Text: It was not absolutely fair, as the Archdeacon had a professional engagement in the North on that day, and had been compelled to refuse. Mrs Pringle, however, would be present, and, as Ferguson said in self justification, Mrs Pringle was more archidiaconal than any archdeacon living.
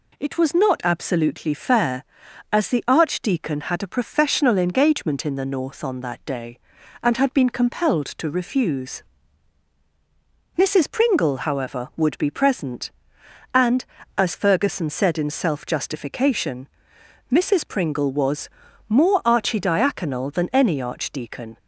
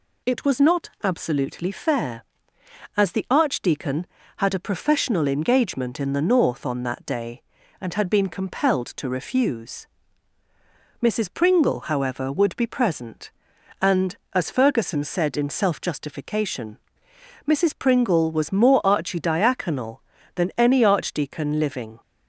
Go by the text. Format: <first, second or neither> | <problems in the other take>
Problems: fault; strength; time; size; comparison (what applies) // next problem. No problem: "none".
second | pauses between "was" and "more"; at 18.4 s; 0.38 s long // stops before "living"; at 21.5 s